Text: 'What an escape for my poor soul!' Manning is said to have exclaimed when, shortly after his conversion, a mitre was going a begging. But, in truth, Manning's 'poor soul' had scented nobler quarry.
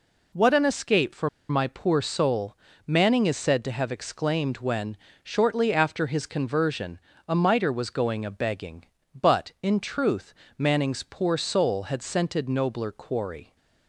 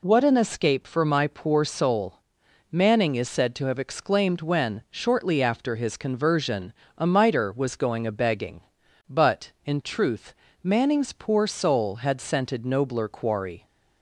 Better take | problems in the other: second | pauses between "for" and "my"; slight; at 1.2 s; 0.20 s long

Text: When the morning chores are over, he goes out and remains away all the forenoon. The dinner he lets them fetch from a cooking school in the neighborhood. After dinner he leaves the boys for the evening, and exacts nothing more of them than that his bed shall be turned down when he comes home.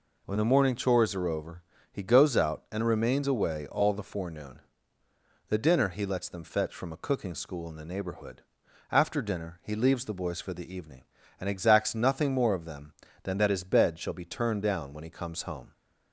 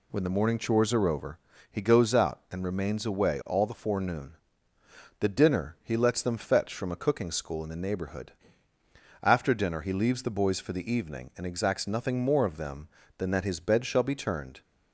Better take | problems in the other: first | stops before "down when he comes home"; at 14.6 s

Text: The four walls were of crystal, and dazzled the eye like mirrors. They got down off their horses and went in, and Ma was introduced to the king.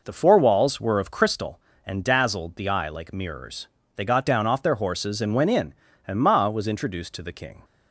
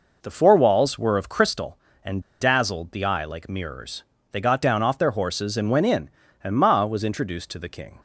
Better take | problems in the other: first | pauses between "and" and "dazzled"; slight; at 2.2 s; 0.17 s long

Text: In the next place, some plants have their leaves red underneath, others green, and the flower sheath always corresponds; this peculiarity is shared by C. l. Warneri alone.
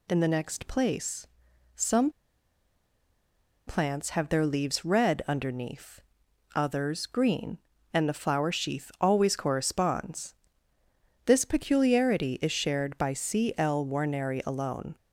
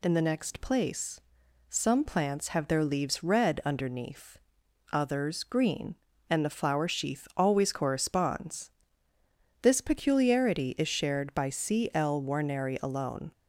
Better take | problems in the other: second | pauses between "some" and "plants"; strong; at 2.0 s; 1.5 s long

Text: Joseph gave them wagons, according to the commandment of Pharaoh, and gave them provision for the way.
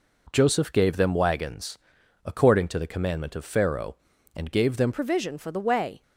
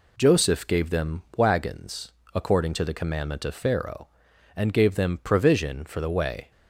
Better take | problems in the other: second | changes voice at "provision"; from 4.9 s on; 1.1 s long

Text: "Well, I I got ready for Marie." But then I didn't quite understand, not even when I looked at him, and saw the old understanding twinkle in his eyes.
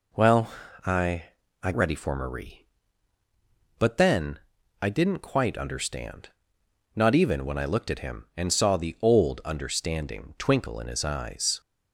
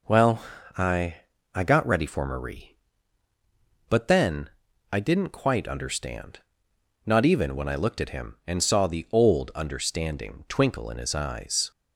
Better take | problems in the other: second | pauses between "I" and "I"; at 1.2 s; 0.40 s long; also in the second // skips "got"; at 1.7 s // pauses between "then" and "I"; at 4.3 s; 0.42 s long; also in the second

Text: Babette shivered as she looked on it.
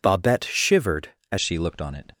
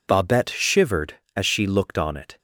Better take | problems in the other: second | changes voice at "she"; from 1.4 s on; 0.7 s long

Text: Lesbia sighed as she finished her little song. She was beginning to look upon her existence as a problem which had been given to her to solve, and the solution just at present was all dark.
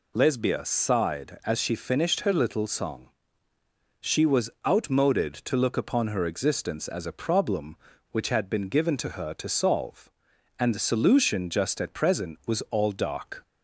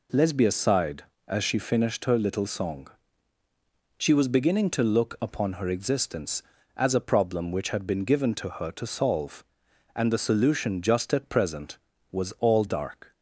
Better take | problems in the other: second | says "outmoded" for "beginning"; at 4.6 s

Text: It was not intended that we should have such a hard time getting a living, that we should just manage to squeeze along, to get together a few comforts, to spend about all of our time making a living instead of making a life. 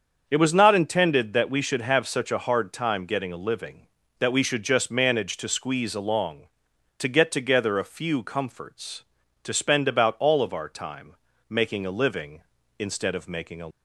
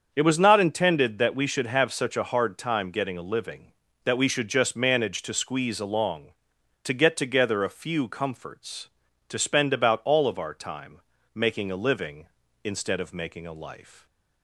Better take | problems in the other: second | starts louder than the rest; until 1.2 s; 7 dB; also in the second // pauses between "time" and "making"; slight; at 11.1 s; 0.34 s long; slight in the second // stops before "life"; at 13.7 s

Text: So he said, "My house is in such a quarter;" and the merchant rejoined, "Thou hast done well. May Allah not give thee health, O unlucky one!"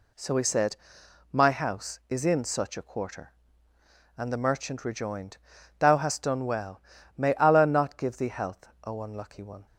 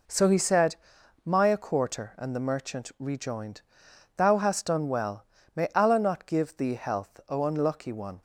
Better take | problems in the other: first | skips "house is in such"; at 1.4 s

